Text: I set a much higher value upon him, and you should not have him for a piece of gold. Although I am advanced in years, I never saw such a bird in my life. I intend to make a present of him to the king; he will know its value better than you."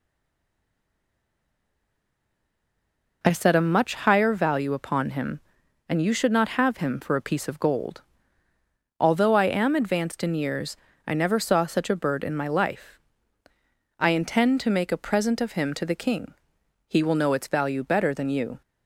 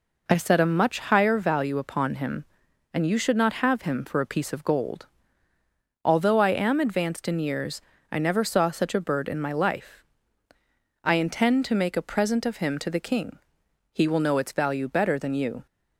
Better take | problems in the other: second | stays silent before the first word; strong; until 3.2 s; 3.2 s long

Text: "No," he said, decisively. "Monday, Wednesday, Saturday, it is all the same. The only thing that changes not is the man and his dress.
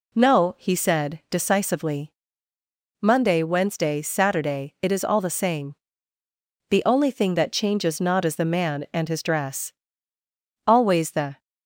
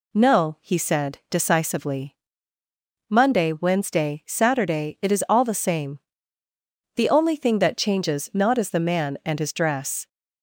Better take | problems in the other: second | goes on to say "Always the"; noticeable; from 10.6 s on; 0.74 s long

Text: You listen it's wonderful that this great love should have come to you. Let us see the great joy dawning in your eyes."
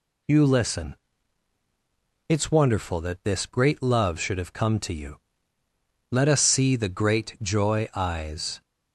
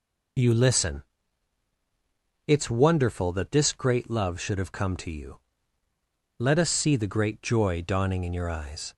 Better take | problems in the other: second | pauses between "listen" and "it's"; strong; at 0.9 s; 1.3 s long; strong in the second // skips "dawning in your"; at 7.9 s

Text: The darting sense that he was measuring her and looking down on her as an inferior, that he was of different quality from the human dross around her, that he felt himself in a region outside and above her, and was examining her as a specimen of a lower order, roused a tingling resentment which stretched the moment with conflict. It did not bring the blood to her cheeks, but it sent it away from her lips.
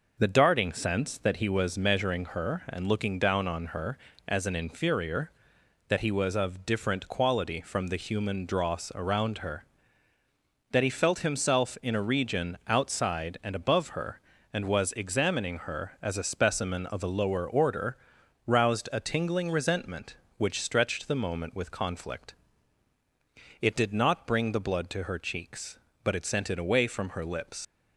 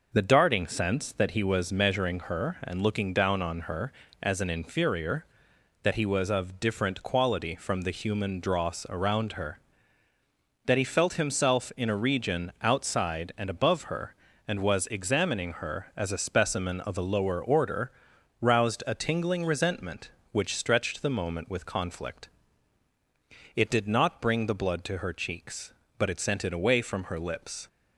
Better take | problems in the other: second | leaves "lips" unfinished; at 27.6 s; 75 ms

